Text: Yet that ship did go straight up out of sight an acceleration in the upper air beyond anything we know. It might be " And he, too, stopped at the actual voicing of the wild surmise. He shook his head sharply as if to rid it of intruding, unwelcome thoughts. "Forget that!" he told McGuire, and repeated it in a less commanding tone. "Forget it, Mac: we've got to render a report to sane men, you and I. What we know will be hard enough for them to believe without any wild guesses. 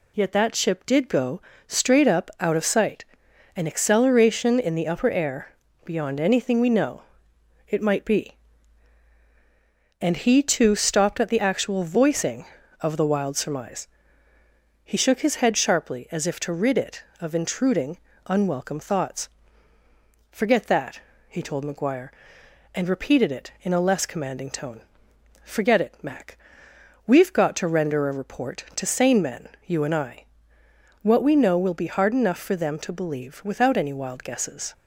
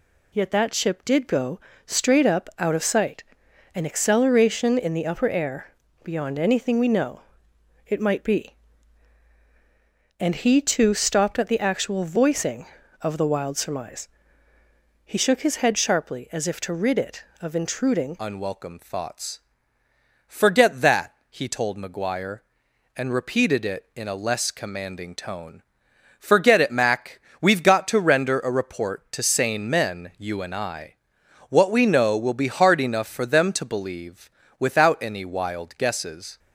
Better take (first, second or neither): first